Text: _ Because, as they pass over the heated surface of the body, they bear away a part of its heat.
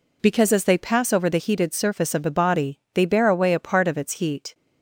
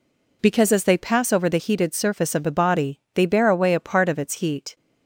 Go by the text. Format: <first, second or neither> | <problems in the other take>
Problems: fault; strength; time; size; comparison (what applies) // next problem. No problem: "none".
neither | none